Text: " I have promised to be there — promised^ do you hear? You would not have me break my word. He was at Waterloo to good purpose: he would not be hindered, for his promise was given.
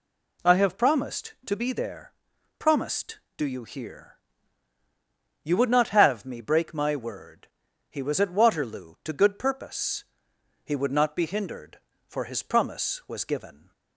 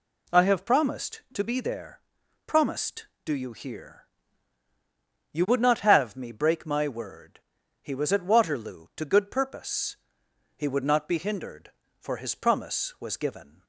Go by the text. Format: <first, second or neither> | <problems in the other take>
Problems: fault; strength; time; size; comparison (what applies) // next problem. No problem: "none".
neither | none